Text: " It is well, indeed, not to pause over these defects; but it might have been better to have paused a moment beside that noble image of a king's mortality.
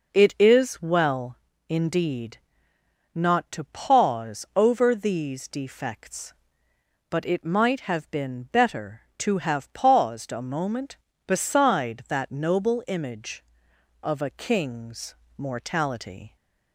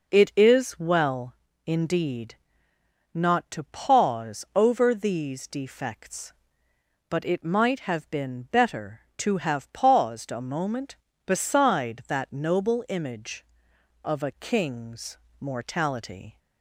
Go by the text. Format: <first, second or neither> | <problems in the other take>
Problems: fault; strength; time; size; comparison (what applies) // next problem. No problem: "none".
neither | pauses between "king's" and "mortality"; slight; the same in both